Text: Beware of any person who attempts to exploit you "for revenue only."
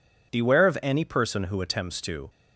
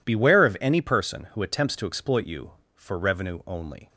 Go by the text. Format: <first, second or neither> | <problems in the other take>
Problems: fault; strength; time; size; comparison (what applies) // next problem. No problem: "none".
second | stops before "exploit you for revenue only"; at 2.2 s